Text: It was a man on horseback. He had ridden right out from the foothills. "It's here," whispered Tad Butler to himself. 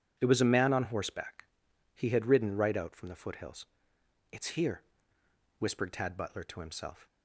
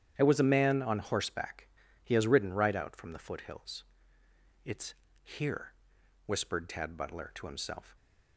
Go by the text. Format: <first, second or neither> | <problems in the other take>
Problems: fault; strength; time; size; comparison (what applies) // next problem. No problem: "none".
first | starts louder than the rest; strong; until 1.1 s; 10 dB // says "has" for "had"; at 2.1 s // pauses between "It's" and "here"; slight; at 4.9 s; 0.30 s long